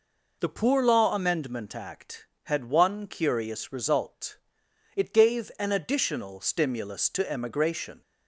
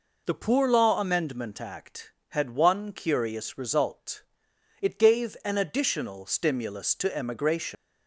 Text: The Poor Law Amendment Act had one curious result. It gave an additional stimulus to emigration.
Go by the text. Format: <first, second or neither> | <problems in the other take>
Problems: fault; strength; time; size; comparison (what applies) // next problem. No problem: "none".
first | leaves "emigration" unfinished; at 7.7 s; 115 ms